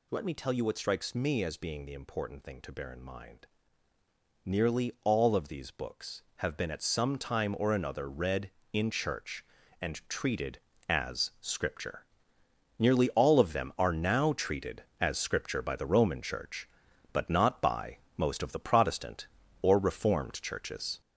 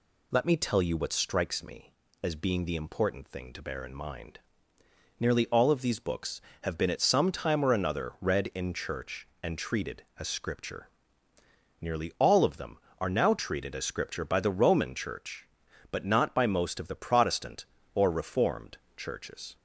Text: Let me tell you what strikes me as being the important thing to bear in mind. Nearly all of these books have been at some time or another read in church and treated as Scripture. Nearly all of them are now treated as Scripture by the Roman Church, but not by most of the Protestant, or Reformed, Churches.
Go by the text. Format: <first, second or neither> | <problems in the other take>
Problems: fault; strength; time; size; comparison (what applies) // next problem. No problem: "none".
second | gets louder; noticeable; throughout; 4.5 dB // pauses between "by" and "most"; slight; at 17.9 s; 0.20 s long